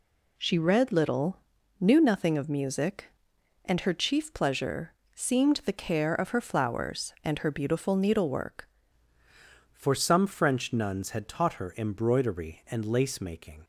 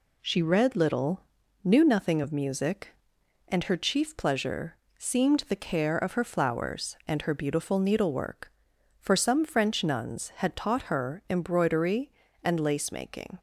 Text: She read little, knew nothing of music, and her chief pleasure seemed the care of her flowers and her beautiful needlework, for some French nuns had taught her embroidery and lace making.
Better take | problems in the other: second | pauses between "pleasure" and "seemed"; slight; at 4.9 s; 0.22 s long; slight in the second // changes voice at "for"; from 9.7 s on; 3.9 s long

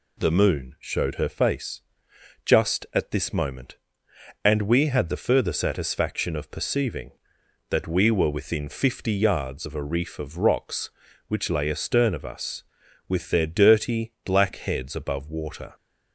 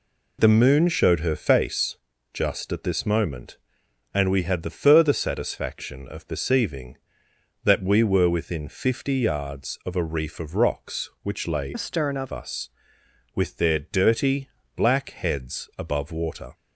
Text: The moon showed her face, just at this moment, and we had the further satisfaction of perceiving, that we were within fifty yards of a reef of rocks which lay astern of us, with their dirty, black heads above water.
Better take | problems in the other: first | changes voice from "astern" to "of"; from 11.7 to 12.3 s; 0.6 s long

